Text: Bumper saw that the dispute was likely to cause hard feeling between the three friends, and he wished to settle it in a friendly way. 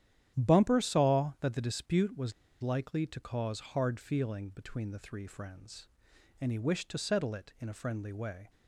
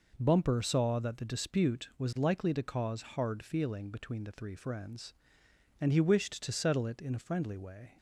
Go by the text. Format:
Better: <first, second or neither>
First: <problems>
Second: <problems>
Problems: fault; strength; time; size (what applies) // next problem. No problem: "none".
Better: second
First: starts louder than the rest; strong; until 1.4 s; 10.5 dB // pauses between "was" and "likely"; slight; at 2.3 s; 0.29 s long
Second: none